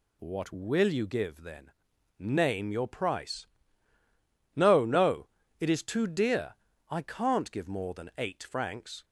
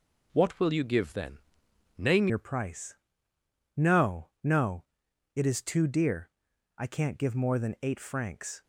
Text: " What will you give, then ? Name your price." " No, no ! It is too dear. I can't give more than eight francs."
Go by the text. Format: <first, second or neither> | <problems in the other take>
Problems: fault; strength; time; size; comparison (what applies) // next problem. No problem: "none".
first | changes voice at "your"; from 2.2 s on; 6.4 s long